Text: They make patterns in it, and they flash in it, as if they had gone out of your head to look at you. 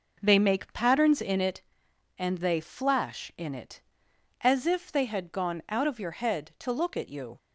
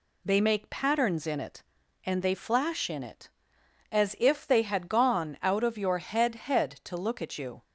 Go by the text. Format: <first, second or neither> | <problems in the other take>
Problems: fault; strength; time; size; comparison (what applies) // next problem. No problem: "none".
first | says "head" twice; at 6.3 s